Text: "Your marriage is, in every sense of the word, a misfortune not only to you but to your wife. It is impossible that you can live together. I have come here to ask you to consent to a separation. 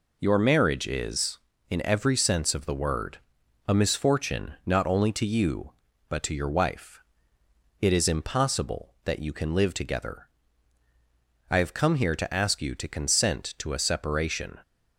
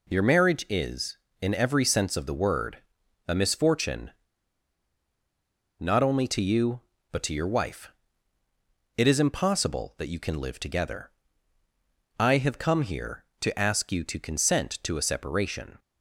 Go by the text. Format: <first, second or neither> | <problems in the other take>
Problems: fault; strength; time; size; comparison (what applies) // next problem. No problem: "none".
first | pauses between "misfortune" and "not"; strong; at 4.1 s; 1.6 s long